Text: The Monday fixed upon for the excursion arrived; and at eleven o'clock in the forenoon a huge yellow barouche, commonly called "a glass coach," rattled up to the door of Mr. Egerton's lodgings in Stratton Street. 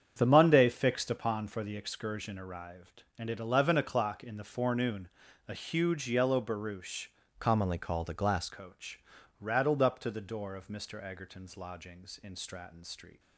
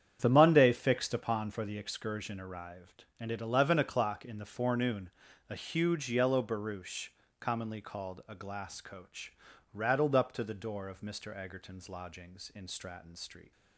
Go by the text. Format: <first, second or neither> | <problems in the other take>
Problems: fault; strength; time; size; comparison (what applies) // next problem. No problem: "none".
second | starts louder than the rest; strong; until 1.1 s; 7.5 dB; strong in the second // pauses between "forenoon" and "a"; at 5.0 s; 0.38 s long; also in the second // changes voice from "commonly" to "glass"; from 7.3 to 8.4 s; 1.1 s long